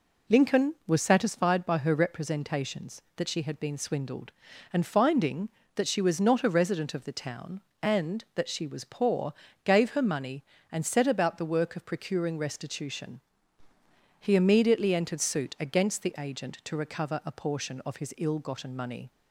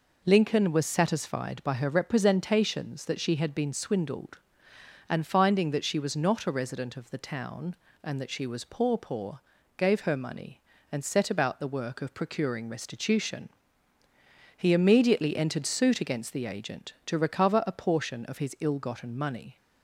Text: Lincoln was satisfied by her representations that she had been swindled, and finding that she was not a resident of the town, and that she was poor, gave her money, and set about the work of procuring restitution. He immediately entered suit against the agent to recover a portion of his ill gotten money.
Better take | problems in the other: first | says "poor" twice; at 8.9 s

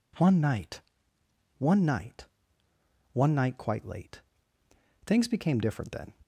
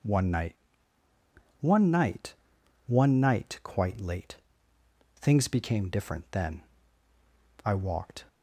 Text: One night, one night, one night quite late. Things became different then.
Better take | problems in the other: first | goes on to say "I walked"; noticeable; from 7.6 s on; 0.62 s long

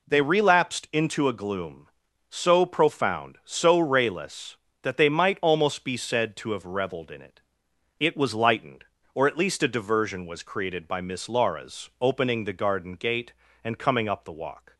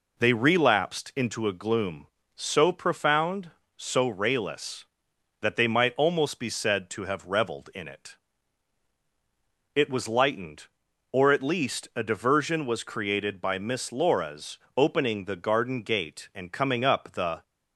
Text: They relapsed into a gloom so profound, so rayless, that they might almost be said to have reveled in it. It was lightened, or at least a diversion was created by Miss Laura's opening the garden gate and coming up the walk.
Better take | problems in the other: first | pauses between "Laura's" and "opening"; slight; at 14.5 s; 0.18 s long // stops before "walk"; at 17.4 s

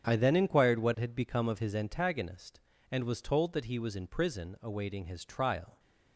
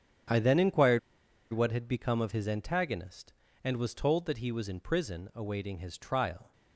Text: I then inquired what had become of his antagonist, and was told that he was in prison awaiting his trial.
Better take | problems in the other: first | starts louder than the rest; strong; until 1.8 s; 8 dB; strong in the first // pauses between "inquired" and "what"; noticeable; at 0.9 s; 0.52 s long

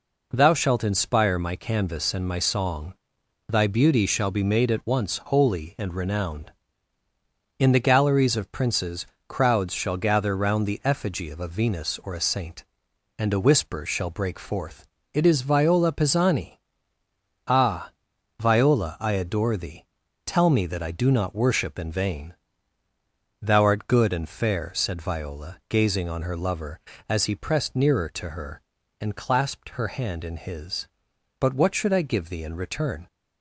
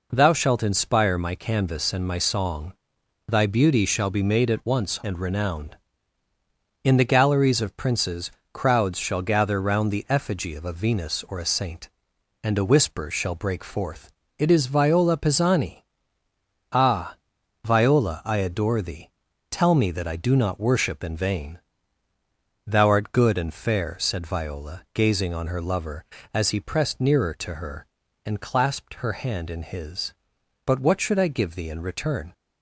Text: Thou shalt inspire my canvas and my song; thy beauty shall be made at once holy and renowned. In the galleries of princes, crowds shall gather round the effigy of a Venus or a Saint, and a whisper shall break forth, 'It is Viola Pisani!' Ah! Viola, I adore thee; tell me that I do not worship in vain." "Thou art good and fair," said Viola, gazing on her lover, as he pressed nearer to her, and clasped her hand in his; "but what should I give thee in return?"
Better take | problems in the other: first | skips "holy"; at 4.9 s

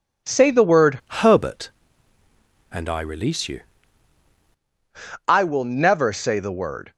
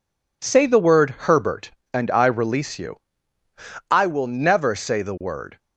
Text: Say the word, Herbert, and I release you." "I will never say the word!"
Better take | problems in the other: second | changes voice from "Herbert" to "you"; from 1.2 to 3.6 s; 2.4 s long

